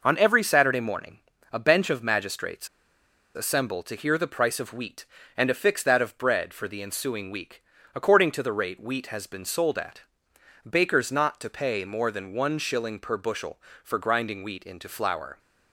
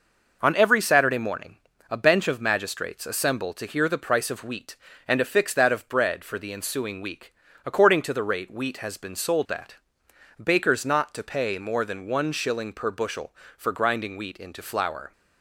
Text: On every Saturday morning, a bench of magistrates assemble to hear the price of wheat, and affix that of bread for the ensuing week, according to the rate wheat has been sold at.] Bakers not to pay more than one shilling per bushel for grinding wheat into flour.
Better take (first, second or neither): second